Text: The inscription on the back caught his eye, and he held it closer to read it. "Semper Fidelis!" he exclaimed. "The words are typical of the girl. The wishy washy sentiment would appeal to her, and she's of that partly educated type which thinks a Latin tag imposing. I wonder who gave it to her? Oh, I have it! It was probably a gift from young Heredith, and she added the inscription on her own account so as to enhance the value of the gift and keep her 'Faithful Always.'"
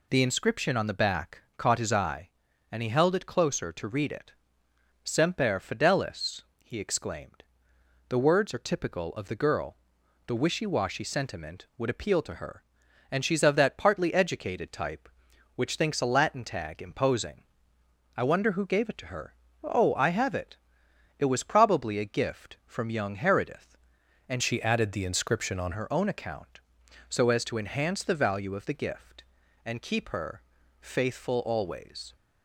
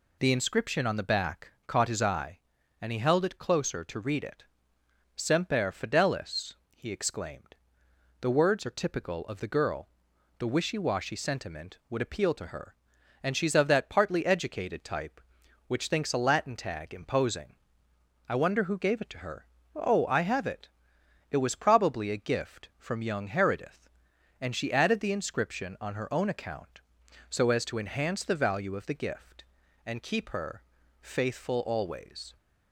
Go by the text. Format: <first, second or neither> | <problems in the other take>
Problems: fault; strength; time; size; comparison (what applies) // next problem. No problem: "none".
second | pauses between "back" and "caught"; slight; at 1.4 s; 0.16 s long; slight in the second // changes voice from "she" to "on"; from 24.4 to 25.7 s; 1.3 s long // pauses between "her" and "Faithful"; at 30.4 s; 0.40 s long; also in the second